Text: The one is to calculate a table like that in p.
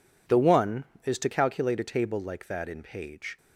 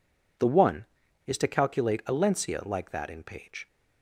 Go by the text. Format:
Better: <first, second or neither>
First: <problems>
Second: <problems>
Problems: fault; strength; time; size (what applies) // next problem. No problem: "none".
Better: first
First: none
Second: says "lencia" for "table"; at 2.1 s